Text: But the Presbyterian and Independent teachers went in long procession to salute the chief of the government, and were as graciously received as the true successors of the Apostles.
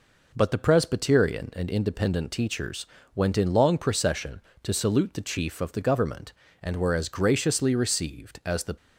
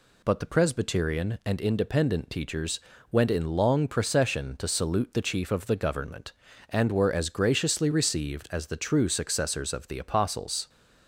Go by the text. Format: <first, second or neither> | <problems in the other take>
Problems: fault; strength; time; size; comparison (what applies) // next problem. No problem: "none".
second | pauses between "teachers" and "went"; slight; at 2.8 s; 0.28 s long; slight in the second // stops before "true successors of the Apostles"; at 8.7 s